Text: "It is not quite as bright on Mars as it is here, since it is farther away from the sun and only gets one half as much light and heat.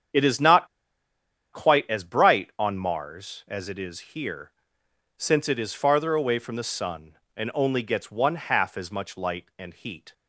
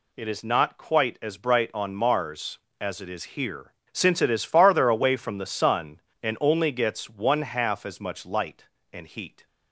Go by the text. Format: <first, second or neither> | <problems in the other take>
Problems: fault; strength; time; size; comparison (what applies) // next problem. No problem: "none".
second | starts louder than the rest; strong; until 2.0 s; 8 dB // pauses between "not" and "quite"; noticeable; at 0.6 s; 0.85 s long